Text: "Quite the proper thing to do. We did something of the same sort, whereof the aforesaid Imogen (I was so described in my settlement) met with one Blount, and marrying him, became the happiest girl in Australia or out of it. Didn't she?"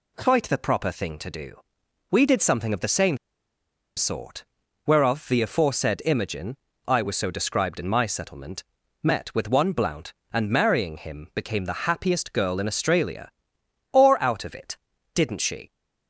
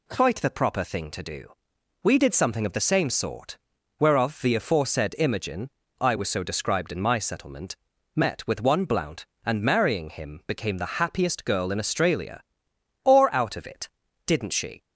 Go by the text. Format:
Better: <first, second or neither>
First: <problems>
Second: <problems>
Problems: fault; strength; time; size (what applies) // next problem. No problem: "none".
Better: second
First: pauses between "same" and "sort"; noticeable; at 3.1 s; 0.79 s long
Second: none